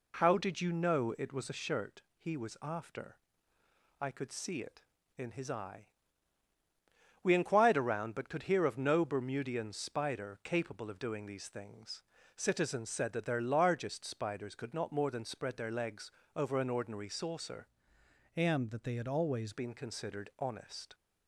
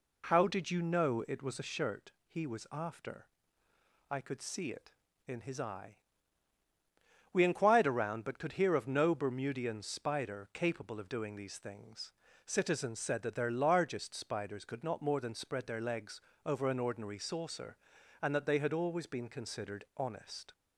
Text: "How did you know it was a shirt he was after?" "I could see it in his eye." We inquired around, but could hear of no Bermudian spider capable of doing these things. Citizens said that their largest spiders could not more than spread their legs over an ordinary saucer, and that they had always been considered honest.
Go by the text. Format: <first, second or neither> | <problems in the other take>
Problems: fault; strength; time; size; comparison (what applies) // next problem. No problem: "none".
second | pauses between "legs" and "over"; slight; at 16.1 s; 0.20 s long; slight in the second // changes voice from "and" to "always"; from 18.3 to 19.5 s; 1.2 s long